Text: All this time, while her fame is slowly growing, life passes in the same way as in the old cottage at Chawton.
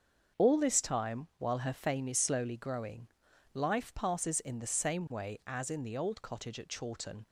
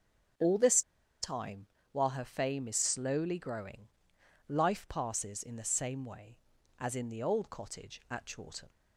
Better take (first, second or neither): first